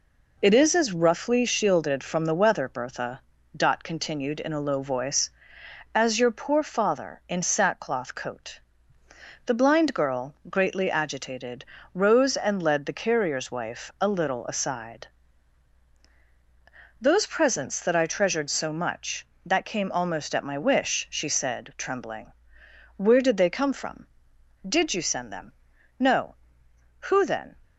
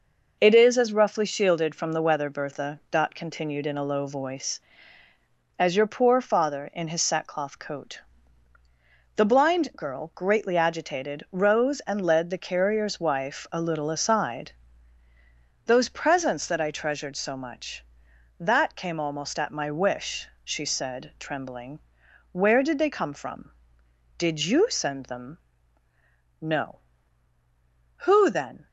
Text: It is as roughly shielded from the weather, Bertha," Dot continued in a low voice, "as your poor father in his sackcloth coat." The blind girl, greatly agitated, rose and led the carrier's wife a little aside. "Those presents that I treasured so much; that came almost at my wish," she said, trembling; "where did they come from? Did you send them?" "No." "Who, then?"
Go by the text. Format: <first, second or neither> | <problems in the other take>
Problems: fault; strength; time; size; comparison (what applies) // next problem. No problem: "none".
second | skips "his"; at 7.4 s